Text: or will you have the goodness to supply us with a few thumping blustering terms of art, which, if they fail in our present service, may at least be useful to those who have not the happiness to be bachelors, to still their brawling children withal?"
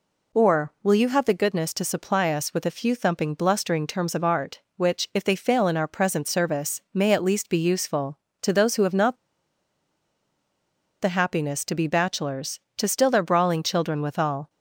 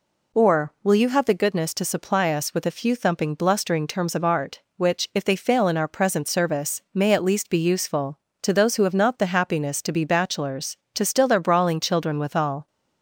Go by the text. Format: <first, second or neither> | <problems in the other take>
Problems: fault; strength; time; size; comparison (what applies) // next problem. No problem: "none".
second | pauses between "not" and "the"; strong; at 9.1 s; 1.8 s long